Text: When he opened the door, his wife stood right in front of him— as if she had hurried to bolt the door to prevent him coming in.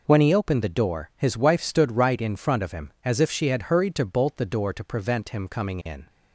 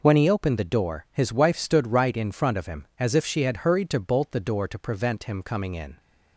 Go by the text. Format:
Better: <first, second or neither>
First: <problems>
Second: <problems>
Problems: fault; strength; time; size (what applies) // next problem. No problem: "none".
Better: neither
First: none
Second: none